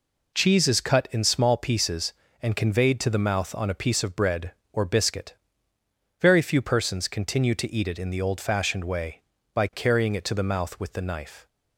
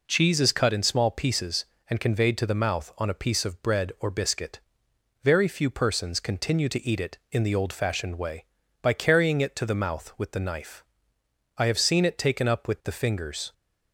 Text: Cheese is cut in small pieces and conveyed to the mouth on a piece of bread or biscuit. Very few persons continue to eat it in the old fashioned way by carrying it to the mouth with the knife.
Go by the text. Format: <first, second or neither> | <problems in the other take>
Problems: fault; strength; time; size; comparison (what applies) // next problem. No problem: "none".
first | goes on to say "I have seen it taken up with the fingers"; strong; from 11.5 s on; 1.9 s long